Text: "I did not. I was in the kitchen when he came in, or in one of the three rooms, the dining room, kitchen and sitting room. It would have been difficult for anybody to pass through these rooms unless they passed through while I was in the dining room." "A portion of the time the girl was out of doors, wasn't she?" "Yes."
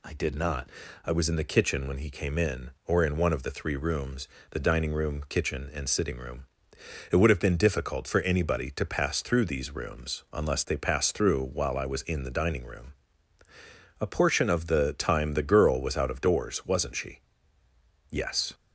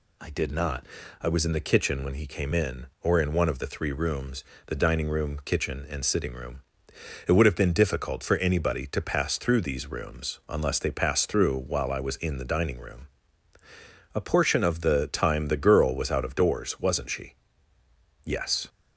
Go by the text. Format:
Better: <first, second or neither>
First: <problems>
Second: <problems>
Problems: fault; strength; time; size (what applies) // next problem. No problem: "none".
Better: neither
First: none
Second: none